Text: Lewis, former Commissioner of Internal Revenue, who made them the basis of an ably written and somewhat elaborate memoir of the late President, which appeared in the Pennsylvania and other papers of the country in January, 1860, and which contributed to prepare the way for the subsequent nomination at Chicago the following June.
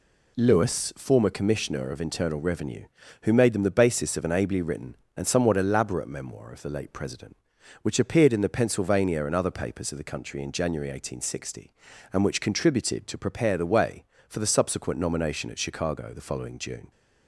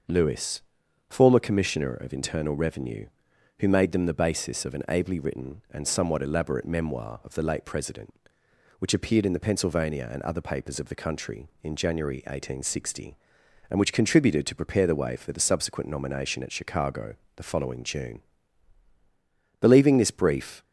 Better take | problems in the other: first | starts louder than the rest; until 1.5 s; 6 dB // pauses between "Chicago" and "the"; slight; at 17.1 s; 0.20 s long // goes on to say "Believing this brief"; noticeable; from 19.6 s on; 1.0 s long

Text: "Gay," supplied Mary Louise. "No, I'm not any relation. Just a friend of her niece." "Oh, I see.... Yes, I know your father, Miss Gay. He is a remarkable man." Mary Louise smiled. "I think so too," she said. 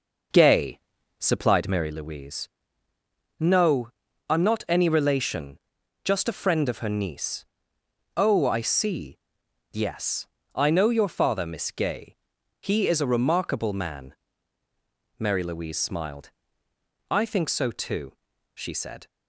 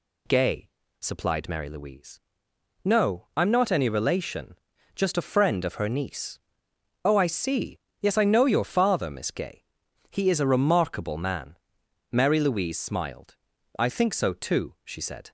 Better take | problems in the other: second | starts louder than the rest; noticeable; until 1.9 s; 5.5 dB

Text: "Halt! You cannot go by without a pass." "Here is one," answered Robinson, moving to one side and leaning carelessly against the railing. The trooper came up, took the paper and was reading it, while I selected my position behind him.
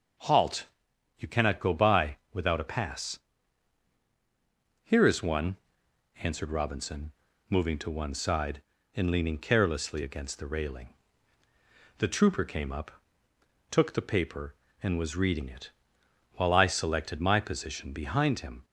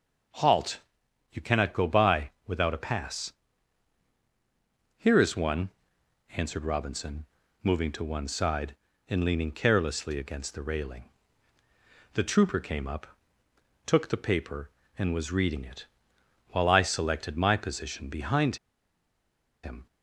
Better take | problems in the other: first | starts louder than the rest; until 1.8 s; 6 dB; also in the first // pauses between "behind" and "him"; at 18.5 s; 1.0 s long

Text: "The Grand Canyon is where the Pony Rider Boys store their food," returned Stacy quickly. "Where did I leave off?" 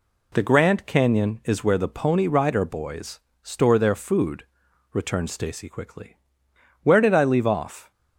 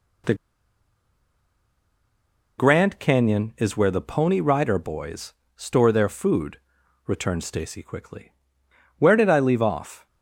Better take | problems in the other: first | pauses between "The" and "Grand"; strong; at 0.3 s; 2.2 s long // pauses between "Boys" and "store"; slight; at 5.3 s; 0.22 s long; slight in the first

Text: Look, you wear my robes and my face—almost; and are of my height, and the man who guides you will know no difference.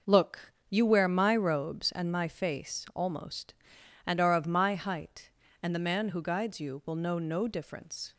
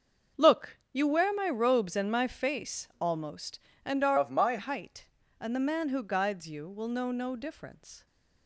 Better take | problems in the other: first | starts louder than the rest; until 1.5 s; 6.5 dB // changes voice from "of" to "my"; from 4.1 to 4.5 s; 0.4 s long

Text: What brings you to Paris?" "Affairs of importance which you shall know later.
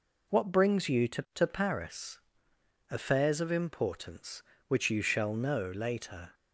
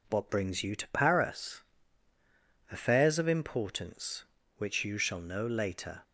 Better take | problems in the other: second | says "to" twice; at 1.3 s

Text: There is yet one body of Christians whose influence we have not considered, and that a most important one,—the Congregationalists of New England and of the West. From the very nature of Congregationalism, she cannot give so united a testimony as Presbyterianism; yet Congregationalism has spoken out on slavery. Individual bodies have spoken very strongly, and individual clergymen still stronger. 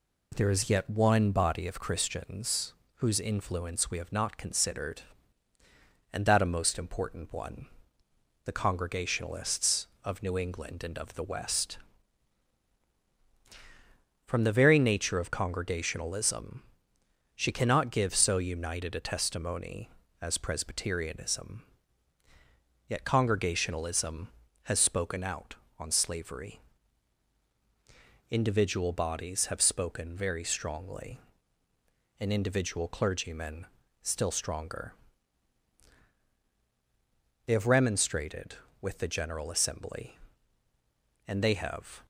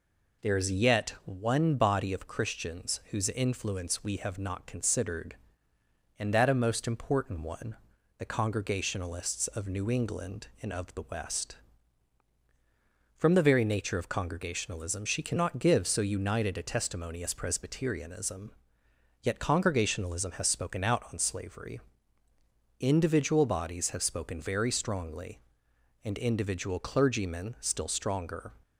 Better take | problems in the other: second | pauses between "Christians" and "whose"; slight; at 2.7 s; 0.24 s long // pauses between "clergymen" and "still"; slight; at 33.6 s; 0.34 s long // goes on to say "They have remonstrated with the General Assembly and they have"; strong; from 37.4 s on; 4.5 s long

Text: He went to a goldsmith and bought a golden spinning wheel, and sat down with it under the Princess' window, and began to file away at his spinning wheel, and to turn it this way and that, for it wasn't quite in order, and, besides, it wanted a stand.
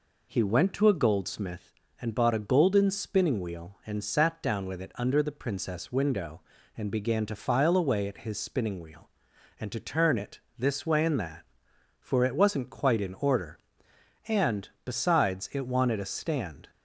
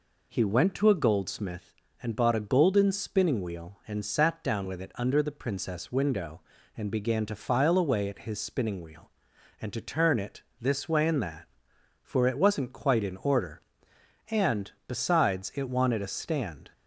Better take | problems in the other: neither | pauses between "it" and "this"; slight; the same in both

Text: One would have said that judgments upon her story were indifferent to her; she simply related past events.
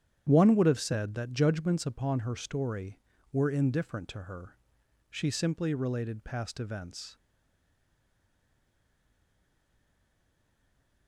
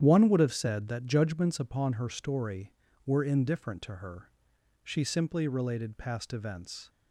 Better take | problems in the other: second | starts louder than the rest; strong; until 1.2 s; 9.5 dB; strong in the second // stays silent after the last word; strong; from 7.1 s on; 3.9 s long

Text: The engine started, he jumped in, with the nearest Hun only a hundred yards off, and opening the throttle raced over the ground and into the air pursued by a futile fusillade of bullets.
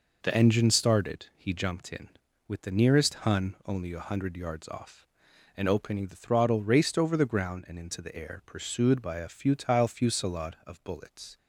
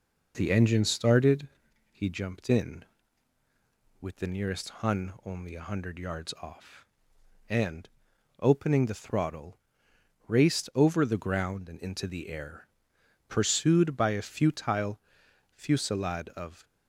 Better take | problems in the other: first | pauses between "and" and "opening"; noticeable; at 7.8 s; 0.50 s long // pauses between "throttle" and "raced"; noticeable; at 9.5 s; 0.72 s long // pauses between "air" and "pursued"; noticeable; at 12.6 s; 0.62 s long // pauses between "futile" and "fusillade"; noticeable; at 14.9 s; 0.54 s long // stops before "bullets"; at 16.6 s

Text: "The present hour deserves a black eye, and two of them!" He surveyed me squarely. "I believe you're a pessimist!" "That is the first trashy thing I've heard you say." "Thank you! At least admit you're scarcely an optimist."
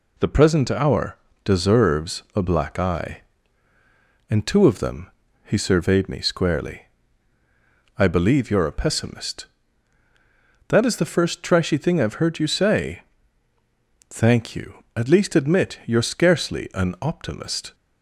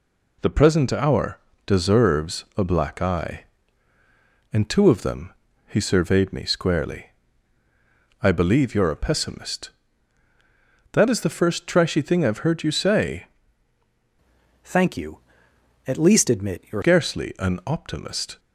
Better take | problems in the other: first | pauses between "hour" and "deserves"; slight; at 1.3 s; 0.30 s long; slight in the first // changes voice from "Thank" to "you're"; from 14.6 to 16.8 s; 2.2 s long

